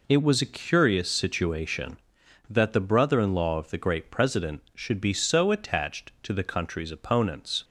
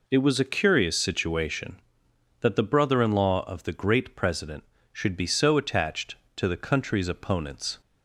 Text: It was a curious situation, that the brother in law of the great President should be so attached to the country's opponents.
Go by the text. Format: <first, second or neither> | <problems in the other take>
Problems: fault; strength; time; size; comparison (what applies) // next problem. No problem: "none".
neither | none